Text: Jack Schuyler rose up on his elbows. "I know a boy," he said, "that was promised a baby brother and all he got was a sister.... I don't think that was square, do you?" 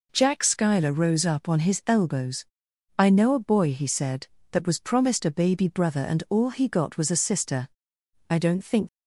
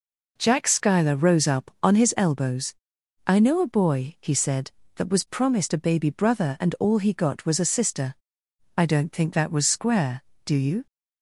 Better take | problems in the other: second | stops before "that was square do you"; at 8.8 s

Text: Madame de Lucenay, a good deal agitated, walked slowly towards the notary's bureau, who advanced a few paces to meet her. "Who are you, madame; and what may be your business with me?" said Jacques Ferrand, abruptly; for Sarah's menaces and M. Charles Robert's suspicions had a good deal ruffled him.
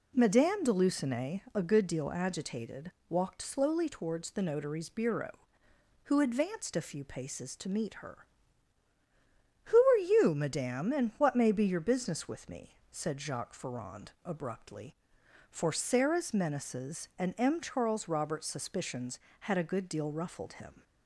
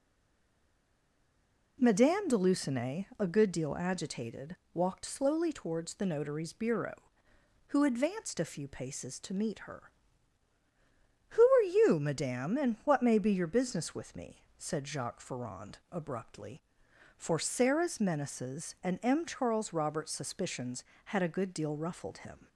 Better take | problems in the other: first | stays silent before the first word; noticeable; until 1.7 s; 1.7 s long

